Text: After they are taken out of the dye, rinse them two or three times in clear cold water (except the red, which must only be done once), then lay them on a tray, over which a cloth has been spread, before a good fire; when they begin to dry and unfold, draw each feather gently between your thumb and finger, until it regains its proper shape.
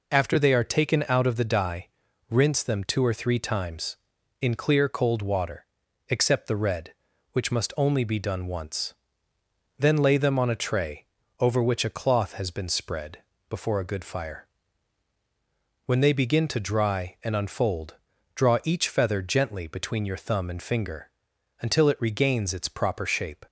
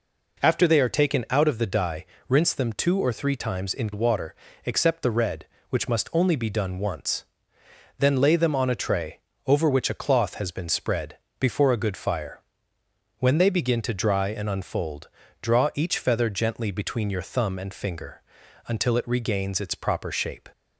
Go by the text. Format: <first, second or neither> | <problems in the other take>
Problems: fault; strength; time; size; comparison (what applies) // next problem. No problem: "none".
first | skips "clear cold"; at 3.9 s